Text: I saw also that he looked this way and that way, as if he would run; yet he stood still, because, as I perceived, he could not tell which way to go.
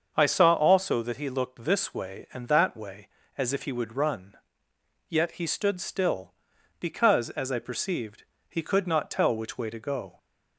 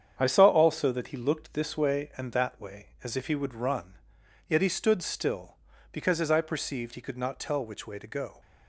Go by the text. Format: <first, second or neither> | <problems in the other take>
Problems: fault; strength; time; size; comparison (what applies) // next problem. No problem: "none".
neither | starts louder than the rest; the same in both